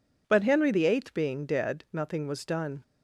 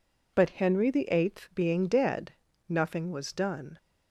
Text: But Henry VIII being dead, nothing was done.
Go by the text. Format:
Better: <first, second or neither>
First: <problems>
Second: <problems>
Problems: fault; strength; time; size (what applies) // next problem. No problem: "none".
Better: neither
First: none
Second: none